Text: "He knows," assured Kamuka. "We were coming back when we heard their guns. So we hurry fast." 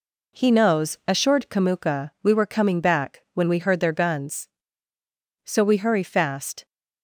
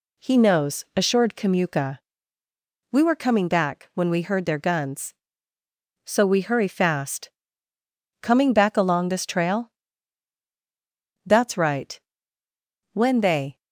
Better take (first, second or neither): first